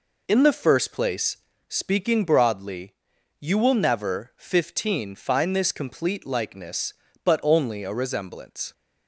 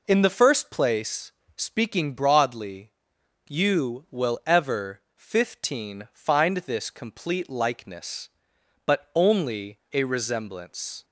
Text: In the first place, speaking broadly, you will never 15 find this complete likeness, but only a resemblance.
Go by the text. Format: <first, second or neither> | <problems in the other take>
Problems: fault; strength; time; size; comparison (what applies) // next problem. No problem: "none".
first | says "ever" for "never"; at 4.4 s